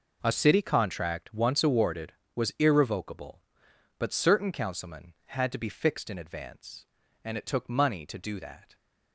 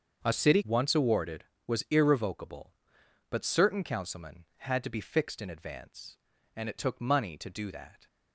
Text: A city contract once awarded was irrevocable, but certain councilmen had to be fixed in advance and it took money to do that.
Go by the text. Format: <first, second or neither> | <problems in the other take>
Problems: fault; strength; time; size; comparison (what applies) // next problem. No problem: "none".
first | starts louder than the rest; until 1.2 s; 7 dB // skips "contract"; at 0.6 s